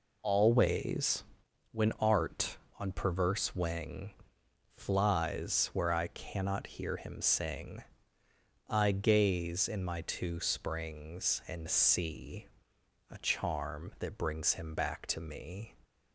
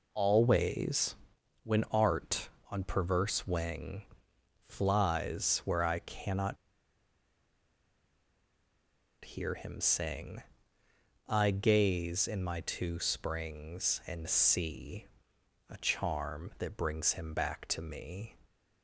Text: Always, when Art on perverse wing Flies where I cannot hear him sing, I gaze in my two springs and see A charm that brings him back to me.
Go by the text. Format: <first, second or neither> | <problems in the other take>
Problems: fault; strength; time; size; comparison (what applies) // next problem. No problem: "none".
first | pauses between "wing" and "Flies"; noticeable; at 4.0 s; 0.62 s long; noticeable in the first // pauses between "cannot" and "hear"; strong; at 6.5 s; 2.6 s long // pauses between "see" and "A"; noticeable; at 15.0 s; 0.64 s long; noticeable in the first